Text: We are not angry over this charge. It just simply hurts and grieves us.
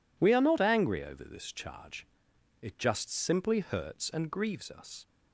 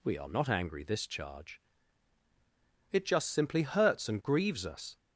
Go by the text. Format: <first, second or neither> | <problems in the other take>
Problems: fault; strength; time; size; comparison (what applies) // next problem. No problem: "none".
first | skips "over"; at 0.8 s